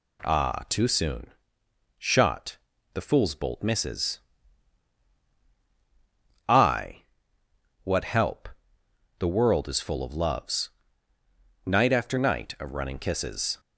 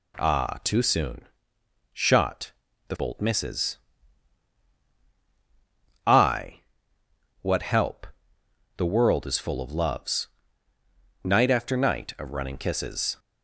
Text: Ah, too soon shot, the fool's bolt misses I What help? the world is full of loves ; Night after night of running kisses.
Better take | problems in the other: first | pauses between "soon" and "shot"; noticeable; at 1.2 s; 0.70 s long; noticeable in the first // skips "fool's"; at 2.9 s // pauses between "misses" and "I"; strong; at 3.7 s; 2.2 s long; strong in the first // pauses between "I" and "What"; noticeable; at 6.6 s; 0.80 s long; noticeable in the first

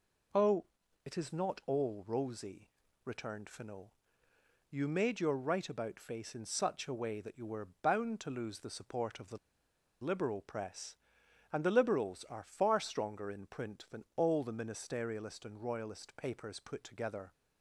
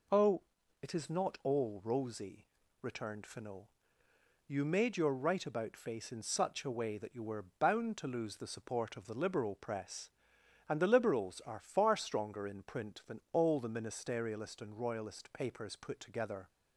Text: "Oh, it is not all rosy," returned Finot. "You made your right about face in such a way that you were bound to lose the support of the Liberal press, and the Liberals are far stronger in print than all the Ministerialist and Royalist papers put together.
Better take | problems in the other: second | pauses between "were" and "bound"; slight; at 7.6 s; 0.16 s long; slight in the second // pauses between "the" and "Liberal"; noticeable; at 9.3 s; 0.66 s long

